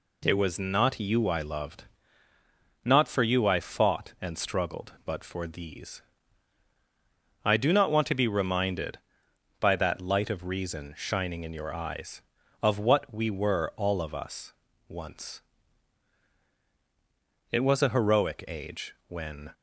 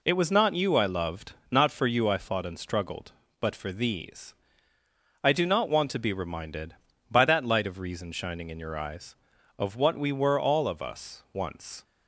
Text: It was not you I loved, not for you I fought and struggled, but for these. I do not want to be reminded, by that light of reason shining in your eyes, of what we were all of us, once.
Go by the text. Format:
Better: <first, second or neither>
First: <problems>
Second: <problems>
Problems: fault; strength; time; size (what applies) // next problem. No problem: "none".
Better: second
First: goes on to say "It was a heroic age when"; strong; from 17.5 s on; 2.0 s long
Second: none